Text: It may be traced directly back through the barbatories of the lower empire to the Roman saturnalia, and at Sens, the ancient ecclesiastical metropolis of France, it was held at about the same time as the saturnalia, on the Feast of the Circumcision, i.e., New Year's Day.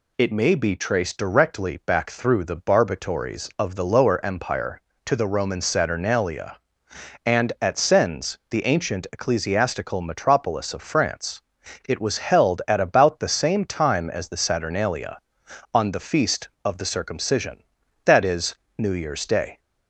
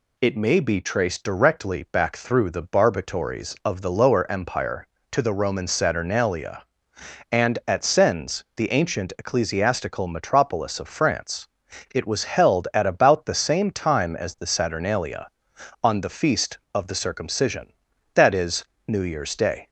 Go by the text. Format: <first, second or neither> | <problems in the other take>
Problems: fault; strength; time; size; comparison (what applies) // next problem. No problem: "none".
neither | none